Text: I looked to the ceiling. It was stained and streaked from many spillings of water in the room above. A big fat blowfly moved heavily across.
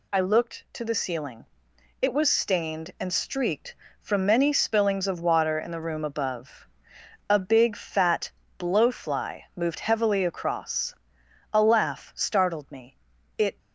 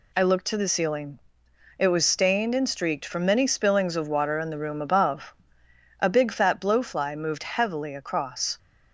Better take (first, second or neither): second